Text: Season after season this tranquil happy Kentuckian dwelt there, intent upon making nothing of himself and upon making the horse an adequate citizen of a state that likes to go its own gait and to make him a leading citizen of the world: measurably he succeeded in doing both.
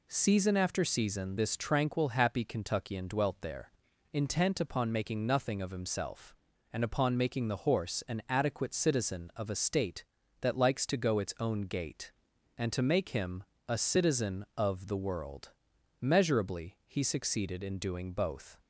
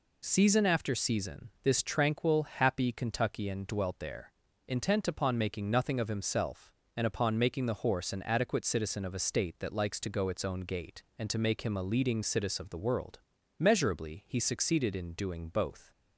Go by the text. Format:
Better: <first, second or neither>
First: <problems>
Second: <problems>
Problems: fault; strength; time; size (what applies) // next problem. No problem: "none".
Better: second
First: pauses between "him" and "a"; slight; at 13.4 s; 0.26 s long // skips "leading"; at 13.7 s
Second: none